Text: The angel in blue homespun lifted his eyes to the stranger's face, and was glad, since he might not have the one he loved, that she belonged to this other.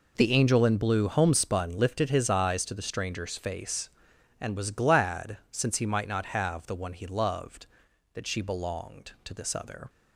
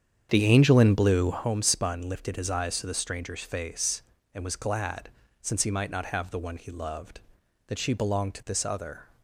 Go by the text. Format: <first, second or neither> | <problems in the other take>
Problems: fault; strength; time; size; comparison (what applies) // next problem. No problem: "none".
first | starts louder than the rest; strong; until 1.5 s; 8 dB